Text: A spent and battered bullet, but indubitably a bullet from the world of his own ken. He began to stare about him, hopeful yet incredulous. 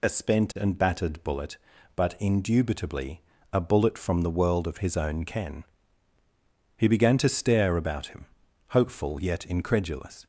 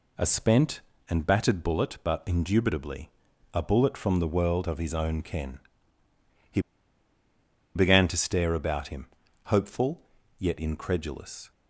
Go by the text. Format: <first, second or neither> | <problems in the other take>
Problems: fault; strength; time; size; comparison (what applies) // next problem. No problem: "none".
first | pauses between "indubitably" and "a"; at 3.0 s; 0.42 s long; slight in the first // pauses between "He" and "began"; at 6.6 s; 1.1 s long // pauses between "hopeful" and "yet"; at 10.0 s; 0.38 s long